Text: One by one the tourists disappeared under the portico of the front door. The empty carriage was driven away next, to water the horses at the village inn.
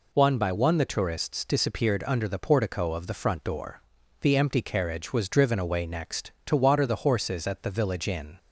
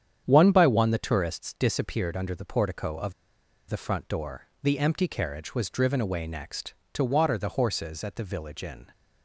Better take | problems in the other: first | starts louder than the rest; strong; until 1.2 s; 8.5 dB // pauses between "of" and "the"; noticeable; at 3.1 s; 0.55 s long

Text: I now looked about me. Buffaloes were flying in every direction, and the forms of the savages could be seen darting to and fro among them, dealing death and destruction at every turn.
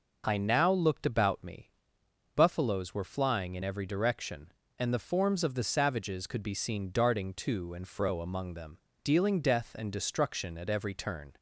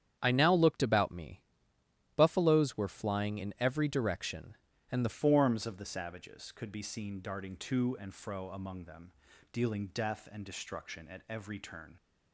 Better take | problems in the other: first | starts louder than the rest; strong; until 1.2 s; 9 dB // changes voice at "forms"; from 5.0 s on; 6.9 s long

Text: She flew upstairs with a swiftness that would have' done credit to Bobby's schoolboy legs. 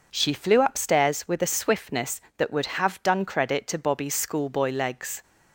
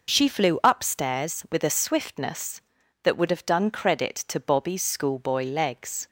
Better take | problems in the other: neither | none

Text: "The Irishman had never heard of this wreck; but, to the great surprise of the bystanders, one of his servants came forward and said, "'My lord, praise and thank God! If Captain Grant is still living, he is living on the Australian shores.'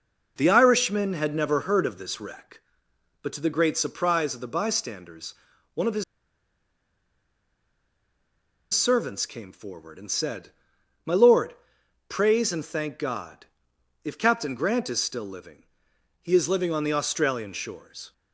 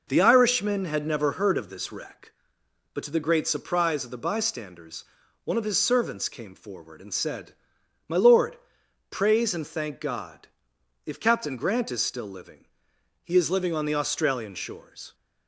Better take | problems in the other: second | pauses between "his" and "servants"; strong; at 6.0 s; 2.7 s long

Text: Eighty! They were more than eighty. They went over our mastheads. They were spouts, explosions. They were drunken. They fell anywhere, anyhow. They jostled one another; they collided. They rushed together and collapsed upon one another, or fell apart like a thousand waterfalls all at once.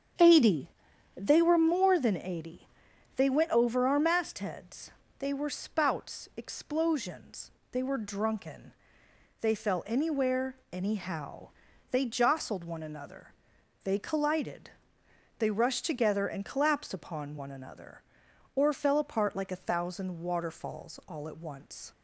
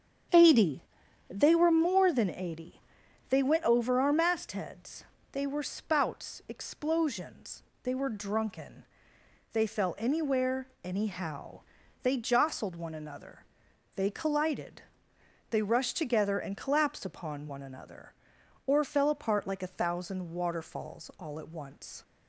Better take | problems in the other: neither | starts louder than the rest; strong; the same in both

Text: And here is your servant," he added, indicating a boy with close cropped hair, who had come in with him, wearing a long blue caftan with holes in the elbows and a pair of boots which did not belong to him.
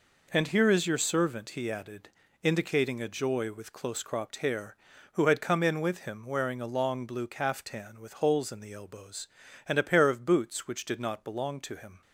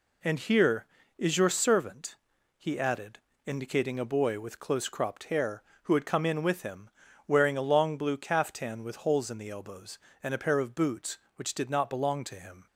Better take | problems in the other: second | says "joy" for "boy"; at 3.0 s

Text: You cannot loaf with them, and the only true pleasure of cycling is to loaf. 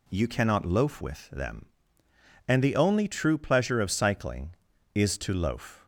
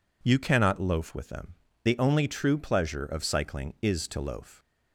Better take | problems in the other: first | skips "and"; at 1.7 s

